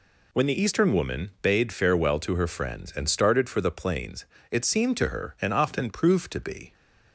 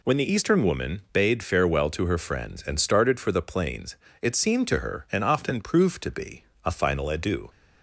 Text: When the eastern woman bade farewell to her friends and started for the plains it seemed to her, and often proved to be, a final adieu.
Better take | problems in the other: second | pauses between "plains" and "it"; slight; at 4.2 s; 0.26 s long; slight in the second // stops before "a final adieu"; at 6.7 s

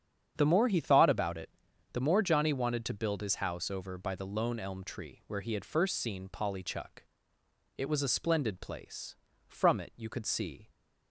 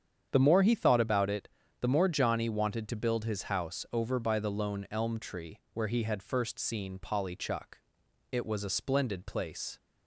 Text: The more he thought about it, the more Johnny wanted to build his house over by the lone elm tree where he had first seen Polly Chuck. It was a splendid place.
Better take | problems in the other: second | starts louder than the rest; strong; until 1.3 s; 8 dB; strong in the second // goes on to say "From it you could see"; noticeable; from 9.4 s on; 1.2 s long

